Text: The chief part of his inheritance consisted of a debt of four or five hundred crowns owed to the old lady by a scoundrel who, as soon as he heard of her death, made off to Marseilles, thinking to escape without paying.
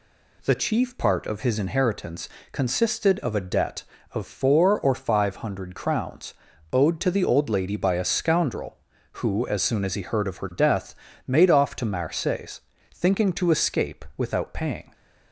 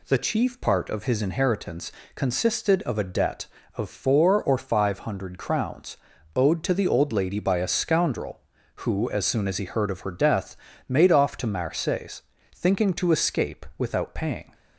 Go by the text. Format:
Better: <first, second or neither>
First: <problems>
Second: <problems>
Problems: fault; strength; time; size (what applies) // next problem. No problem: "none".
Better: neither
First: pauses between "inheritance" and "consisted"; slight; at 2.2 s; 0.24 s long // pauses between "crowns" and "owed"; at 6.3 s; 0.40 s long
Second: pauses between "inheritance" and "consisted"; slight; at 1.8 s; 0.24 s long // pauses between "crowns" and "owed"; at 5.9 s; 0.40 s long